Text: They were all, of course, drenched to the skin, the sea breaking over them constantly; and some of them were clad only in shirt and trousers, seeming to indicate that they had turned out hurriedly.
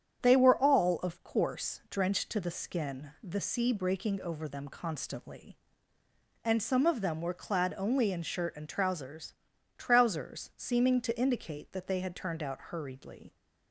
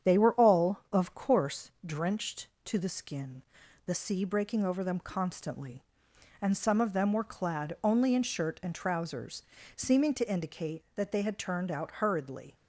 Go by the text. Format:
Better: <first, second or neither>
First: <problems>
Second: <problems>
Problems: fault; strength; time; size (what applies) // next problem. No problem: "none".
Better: second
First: starts louder than the rest; strong; until 1.2 s; 8.5 dB // says "trousers" twice; at 9.7 s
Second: starts louder than the rest; strong; until 1.1 s; 8.5 dB